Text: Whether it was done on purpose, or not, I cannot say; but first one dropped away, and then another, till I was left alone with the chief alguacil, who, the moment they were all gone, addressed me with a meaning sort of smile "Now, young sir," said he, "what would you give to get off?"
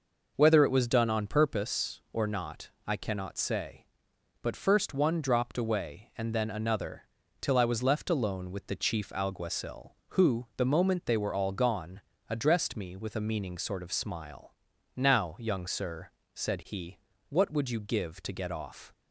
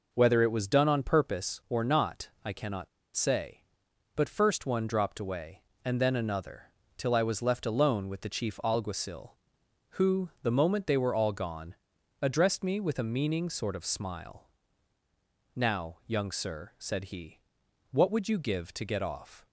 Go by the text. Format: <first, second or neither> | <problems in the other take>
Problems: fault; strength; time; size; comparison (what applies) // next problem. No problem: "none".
first | pauses between "cannot" and "say"; slight; at 2.8 s; 0.28 s long // pauses between "smile" and "Now"; at 14.4 s; 1.0 s long; also in the first